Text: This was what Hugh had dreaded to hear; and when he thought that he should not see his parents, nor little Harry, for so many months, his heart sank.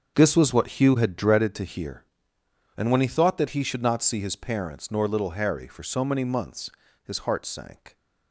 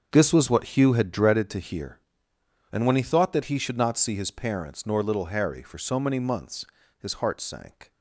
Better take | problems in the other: neither | starts louder than the rest; strong; the same in both

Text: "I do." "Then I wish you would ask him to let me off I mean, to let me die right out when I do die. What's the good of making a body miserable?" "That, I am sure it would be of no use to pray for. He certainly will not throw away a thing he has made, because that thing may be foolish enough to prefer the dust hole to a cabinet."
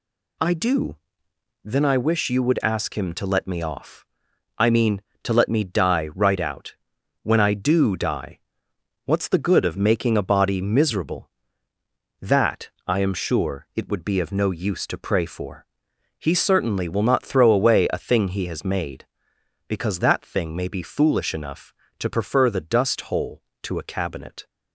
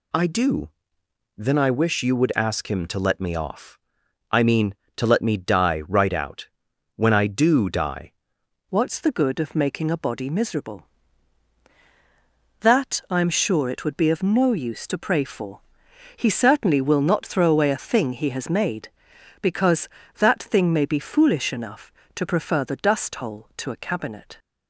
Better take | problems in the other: first | pauses between "off" and "I"; noticeable; at 3.7 s; 0.54 s long; noticeable in the first // pauses between "out" and "when"; noticeable; at 6.4 s; 0.46 s long; noticeable in the first // changes voice at "What's"; from 8.7 s on; 15.6 s long

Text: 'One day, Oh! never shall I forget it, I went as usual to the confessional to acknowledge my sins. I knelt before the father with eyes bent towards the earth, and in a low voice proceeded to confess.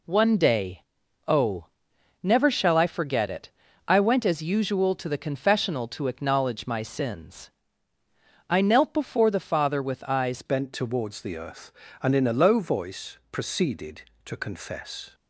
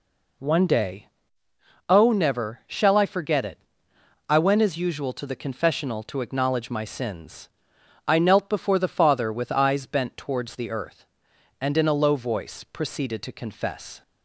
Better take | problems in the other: second | changes voice at "bent"; from 10.4 s on; 4.7 s long

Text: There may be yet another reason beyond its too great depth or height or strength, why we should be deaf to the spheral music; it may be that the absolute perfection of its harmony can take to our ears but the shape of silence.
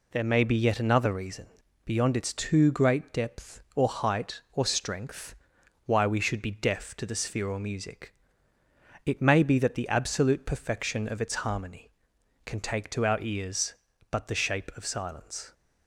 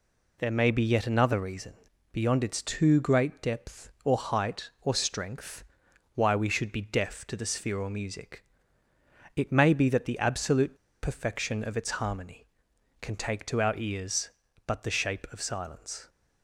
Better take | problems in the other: first | pauses between "reason" and "beyond"; at 1.7 s; 0.40 s long; also in the first // pauses between "absolute" and "perfection"; slight; at 10.7 s; 0.25 s long

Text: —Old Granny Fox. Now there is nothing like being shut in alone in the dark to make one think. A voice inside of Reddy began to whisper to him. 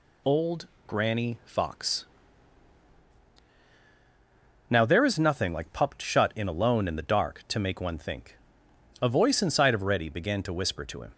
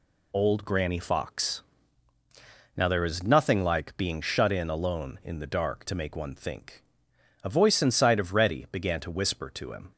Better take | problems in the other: second | pauses between "Old" and "Granny"; slight; at 0.6 s; 0.18 s long // says "pupped" for "being"; at 5.7 s

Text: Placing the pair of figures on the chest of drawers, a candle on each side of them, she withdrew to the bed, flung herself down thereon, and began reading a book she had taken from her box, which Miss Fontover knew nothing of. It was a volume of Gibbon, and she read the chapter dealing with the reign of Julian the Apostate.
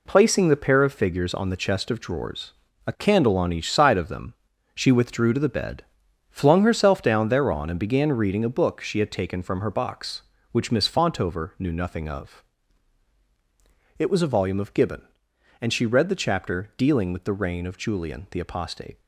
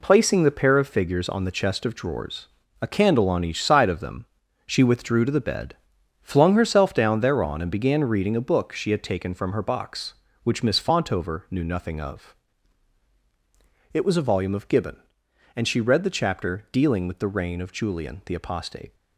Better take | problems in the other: neither | none

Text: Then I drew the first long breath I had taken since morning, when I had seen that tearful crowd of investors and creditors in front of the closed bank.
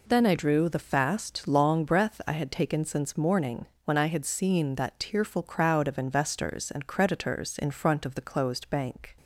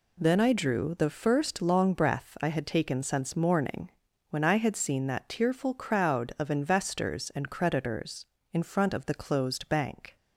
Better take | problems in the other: second | says "fast" for "first"; at 0.7 s

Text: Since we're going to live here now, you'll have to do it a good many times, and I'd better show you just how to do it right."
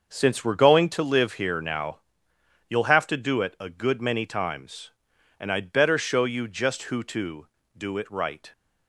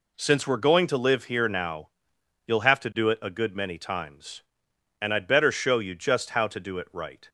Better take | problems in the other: second | starts louder than the rest; until 1.1 s; 6.5 dB // says "who" for "how"; at 6.8 s

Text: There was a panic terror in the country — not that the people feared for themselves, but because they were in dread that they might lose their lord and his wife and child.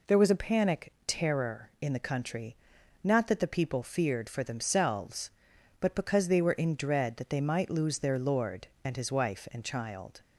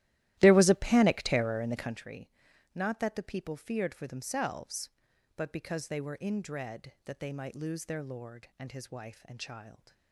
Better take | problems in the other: first | starts louder than the rest; strong; until 2.0 s; 15 dB

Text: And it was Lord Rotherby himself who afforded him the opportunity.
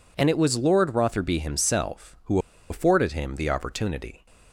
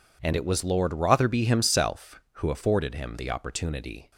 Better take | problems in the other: second | pauses between "who" and "afforded"; slight; at 2.3 s; 0.31 s long

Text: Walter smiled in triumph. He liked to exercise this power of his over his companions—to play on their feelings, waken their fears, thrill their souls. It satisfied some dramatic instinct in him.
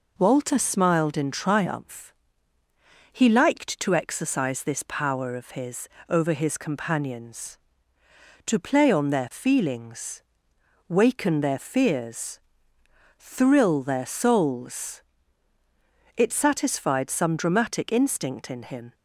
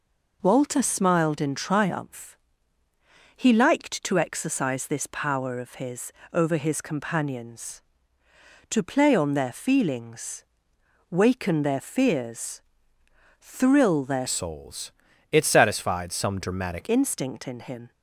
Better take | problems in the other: first | pauses between "his" and "over"; slight; at 6.1 s; 0.20 s long; slight in the first // changes voice from "souls" to "dramatic"; from 14.2 to 16.8 s; 2.6 s long

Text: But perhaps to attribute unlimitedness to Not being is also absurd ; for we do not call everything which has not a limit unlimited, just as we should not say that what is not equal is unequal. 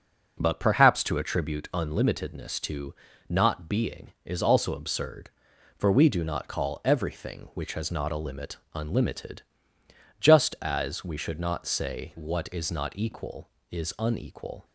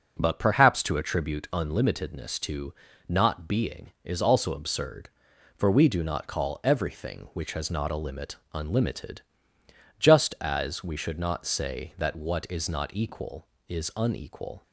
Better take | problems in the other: second | pauses between "to" and "Not"; slight; at 2.9 s; 0.34 s long; slight in the second // pauses between "limit" and "unlimited"; slight; at 8.5 s; 0.18 s long; slight in the second // skips "that"; at 12.1 s

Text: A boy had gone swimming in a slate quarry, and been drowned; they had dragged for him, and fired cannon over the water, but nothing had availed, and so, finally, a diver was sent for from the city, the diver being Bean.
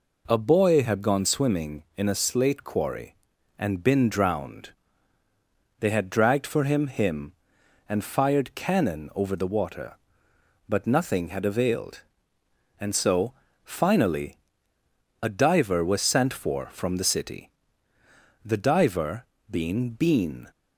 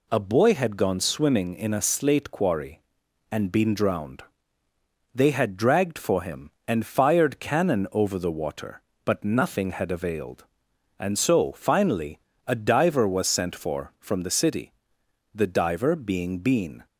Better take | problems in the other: second | says "him" twice; at 6.8 s // pauses between "diver" and "being"; slight; at 19.2 s; 0.24 s long

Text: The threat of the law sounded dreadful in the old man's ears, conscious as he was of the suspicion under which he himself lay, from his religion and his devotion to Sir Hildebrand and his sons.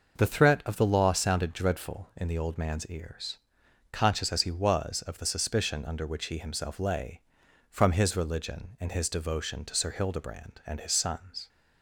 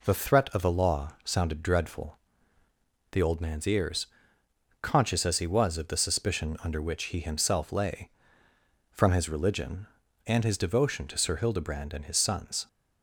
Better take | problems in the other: first | skips "in"; at 2.6 s

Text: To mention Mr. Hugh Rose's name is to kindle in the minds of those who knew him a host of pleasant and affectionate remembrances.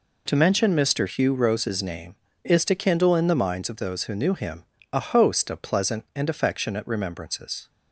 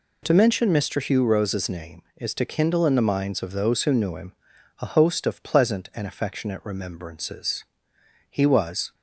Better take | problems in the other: first | pauses between "him" and "a"; noticeable; at 4.3 s; 0.48 s long; slight in the first // goes on to say "He was"; noticeable; from 8.2 s on; 0.64 s long

